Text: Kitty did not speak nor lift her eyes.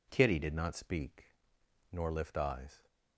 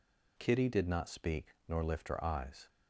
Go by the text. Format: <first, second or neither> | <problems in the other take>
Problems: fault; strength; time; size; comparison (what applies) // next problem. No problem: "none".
second | pauses between "speak" and "nor"; noticeable; at 1.2 s; 0.66 s long // skips "her"; at 2.3 s